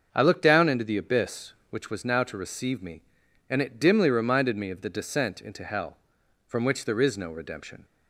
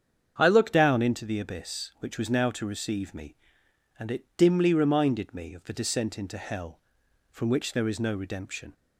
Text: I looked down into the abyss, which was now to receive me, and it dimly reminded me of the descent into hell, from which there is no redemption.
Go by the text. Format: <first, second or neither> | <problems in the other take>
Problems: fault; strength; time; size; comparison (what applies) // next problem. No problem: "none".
first | starts louder than the rest; strong; until 1.3 s; 8 dB; also in the first // changes voice at "down"; from 0.7 s on; 8.0 s long